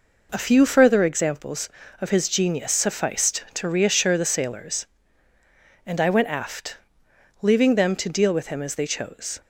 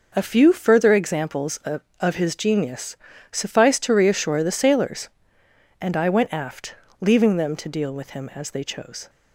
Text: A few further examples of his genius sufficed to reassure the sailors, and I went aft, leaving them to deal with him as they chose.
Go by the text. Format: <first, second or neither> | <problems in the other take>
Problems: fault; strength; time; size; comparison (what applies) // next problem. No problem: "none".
first | says "of" twice; at 1.9 s // pauses between "genius" and "sufficed"; slight; at 2.9 s; 0.36 s long